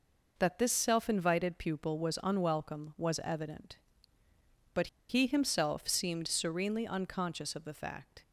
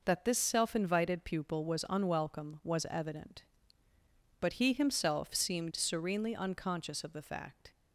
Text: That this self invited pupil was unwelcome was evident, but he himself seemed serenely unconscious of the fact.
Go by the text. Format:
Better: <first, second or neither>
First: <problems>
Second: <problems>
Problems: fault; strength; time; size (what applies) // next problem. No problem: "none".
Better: second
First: pauses between "but" and "he"; slight; at 4.8 s; 0.21 s long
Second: none